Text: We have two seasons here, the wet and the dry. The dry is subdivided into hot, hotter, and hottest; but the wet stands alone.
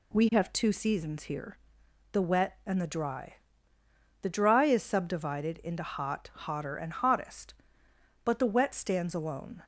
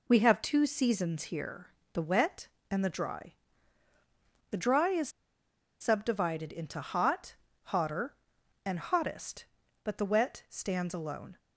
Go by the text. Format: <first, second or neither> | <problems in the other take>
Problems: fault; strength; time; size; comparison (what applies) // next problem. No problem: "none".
first | pauses between "is" and "subdivided"; noticeable; at 5.0 s; 0.71 s long